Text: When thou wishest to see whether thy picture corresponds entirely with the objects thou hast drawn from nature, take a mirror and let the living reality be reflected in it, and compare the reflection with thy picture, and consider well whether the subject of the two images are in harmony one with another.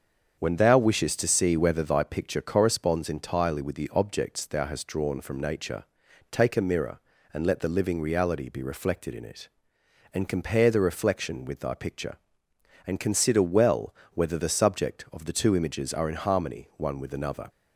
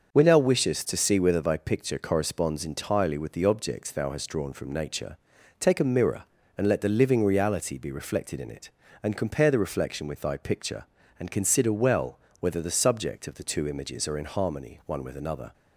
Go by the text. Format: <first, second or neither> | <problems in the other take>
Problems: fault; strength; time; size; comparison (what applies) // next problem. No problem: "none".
neither | starts louder than the rest; the same in both // pauses between "well" and "whether"; slight; the same in both